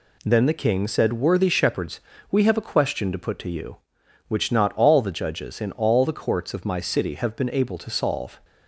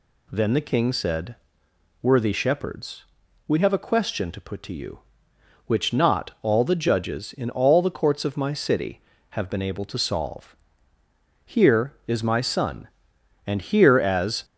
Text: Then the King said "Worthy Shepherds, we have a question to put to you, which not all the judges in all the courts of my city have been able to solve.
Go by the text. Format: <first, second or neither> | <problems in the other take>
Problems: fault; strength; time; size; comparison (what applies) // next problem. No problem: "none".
first | pauses between "said" and "Worthy"; noticeable; at 1.3 s; 0.68 s long // goes on to say "Here is my son and here as"; strong; from 11.4 s on; 3.0 s long